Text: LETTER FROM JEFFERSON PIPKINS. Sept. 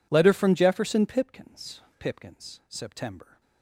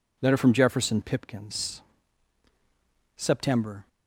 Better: second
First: says "PIPKINS" twice; at 2.0 s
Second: none

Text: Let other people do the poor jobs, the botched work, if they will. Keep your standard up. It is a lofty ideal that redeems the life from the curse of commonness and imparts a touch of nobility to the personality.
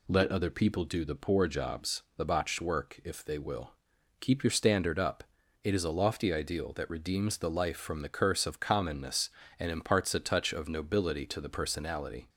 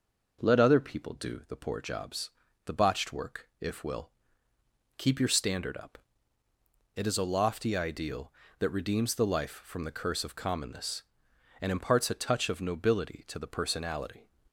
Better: first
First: none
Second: skips "they"; at 3.8 s

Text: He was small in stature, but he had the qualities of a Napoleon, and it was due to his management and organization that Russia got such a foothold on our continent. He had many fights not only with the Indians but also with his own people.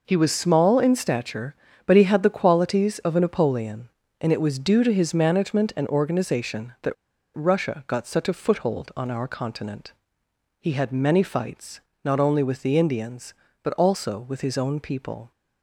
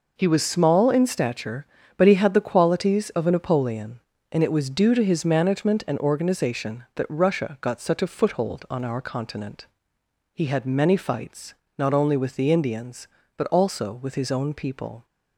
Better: second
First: pauses between "that" and "Russia"; at 6.9 s; 0.41 s long // pauses between "fights" and "not"; slight; at 11.8 s; 0.22 s long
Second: pauses between "fights" and "not"; slight; at 11.5 s; 0.22 s long

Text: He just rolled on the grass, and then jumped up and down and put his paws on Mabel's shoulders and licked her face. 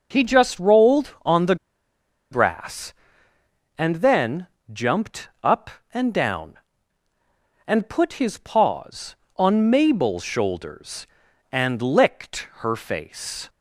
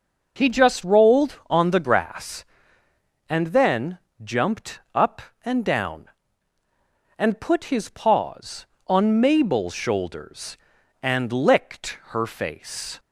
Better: second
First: pauses between "the" and "grass"; noticeable; at 1.5 s; 0.75 s long // pauses between "then" and "jumped"; slight; at 4.4 s; 0.26 s long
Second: pauses between "then" and "jumped"; slight; at 3.9 s; 0.26 s long

